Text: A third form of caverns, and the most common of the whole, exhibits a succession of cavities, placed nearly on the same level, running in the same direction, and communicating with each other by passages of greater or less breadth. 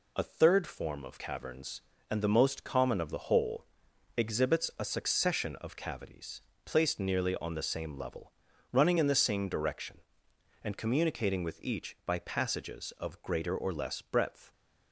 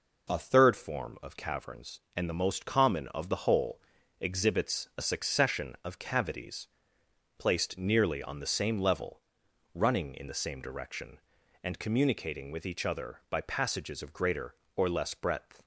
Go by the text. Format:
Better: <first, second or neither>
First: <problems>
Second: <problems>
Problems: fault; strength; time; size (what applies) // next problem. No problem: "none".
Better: second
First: skips "other"; at 11.9 s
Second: none